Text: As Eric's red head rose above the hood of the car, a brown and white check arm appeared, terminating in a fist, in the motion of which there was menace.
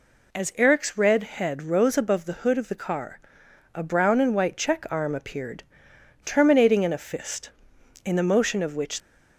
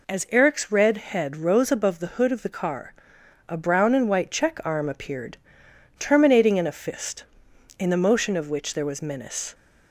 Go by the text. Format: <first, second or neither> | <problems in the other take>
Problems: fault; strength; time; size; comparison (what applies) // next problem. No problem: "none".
second | stops before "there was menace"; at 9.0 s